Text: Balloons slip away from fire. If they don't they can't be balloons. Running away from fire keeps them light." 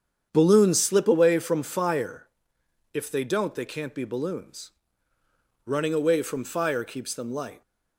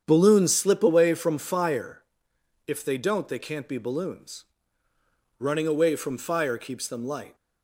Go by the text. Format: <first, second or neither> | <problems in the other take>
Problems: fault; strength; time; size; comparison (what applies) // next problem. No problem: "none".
neither | starts louder than the rest; strong; the same in both